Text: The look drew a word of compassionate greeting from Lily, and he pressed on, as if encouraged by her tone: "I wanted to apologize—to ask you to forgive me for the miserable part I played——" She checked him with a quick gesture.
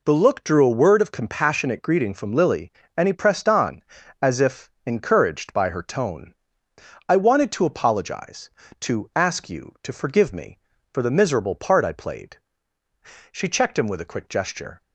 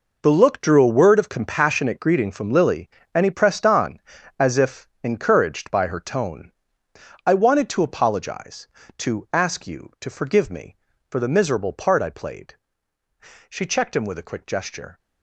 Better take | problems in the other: first | gets quieter; strong; throughout; 12.5 dB // pauses between "if" and "encouraged"; slight; at 4.8 s; 0.16 s long; slight in the first

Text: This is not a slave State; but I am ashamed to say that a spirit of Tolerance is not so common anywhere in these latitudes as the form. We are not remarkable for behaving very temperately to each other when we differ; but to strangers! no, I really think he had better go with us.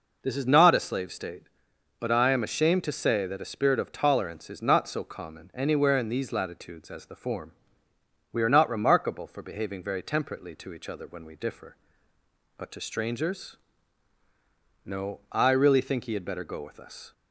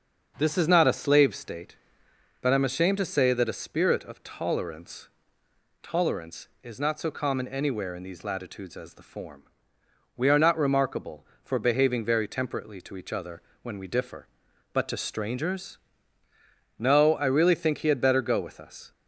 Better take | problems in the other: first | starts louder than the rest; until 1.3 s; 6.5 dB // says "Tolerance" twice; at 5.8 s // pauses between "other" and "when"; slight; at 13.4 s; 0.22 s long

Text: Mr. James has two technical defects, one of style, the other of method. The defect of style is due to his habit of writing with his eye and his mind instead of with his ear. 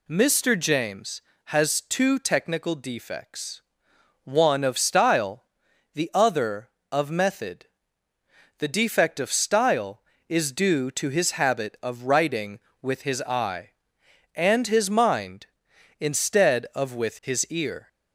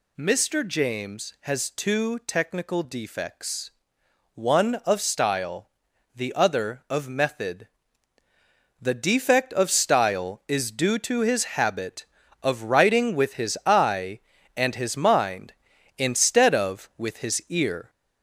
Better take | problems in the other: first | gets louder; noticeable; throughout; 4.5 dB

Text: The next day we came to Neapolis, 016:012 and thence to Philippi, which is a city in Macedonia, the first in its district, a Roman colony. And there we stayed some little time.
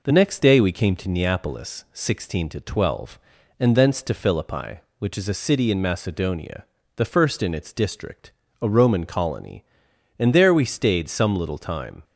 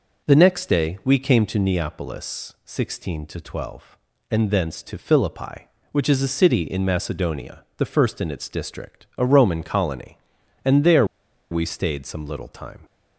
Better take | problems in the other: first | pauses between "there" and "we"; noticeable; at 11.0 s; 0.46 s long

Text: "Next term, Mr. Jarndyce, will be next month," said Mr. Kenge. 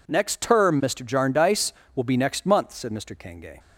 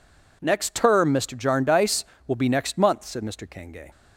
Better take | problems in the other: neither | none

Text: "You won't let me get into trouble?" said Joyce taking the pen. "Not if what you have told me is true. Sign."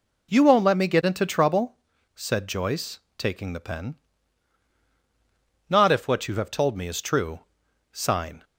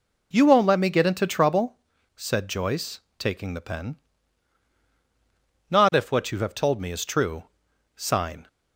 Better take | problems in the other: neither | pauses between "Joyce" and "taking"; slight; the same in both

